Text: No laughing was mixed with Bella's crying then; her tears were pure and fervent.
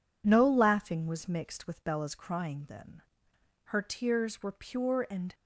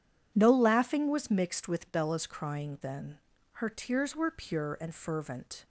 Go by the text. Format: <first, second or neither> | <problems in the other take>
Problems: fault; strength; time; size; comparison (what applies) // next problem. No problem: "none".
second | stops before "fervent"; at 5.3 s